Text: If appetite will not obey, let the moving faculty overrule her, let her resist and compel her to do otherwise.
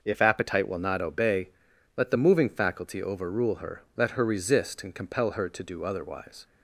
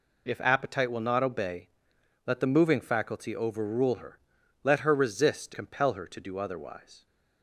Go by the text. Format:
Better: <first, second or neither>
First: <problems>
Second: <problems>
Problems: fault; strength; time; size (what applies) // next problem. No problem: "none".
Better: first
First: none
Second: skips "and"; at 5.5 s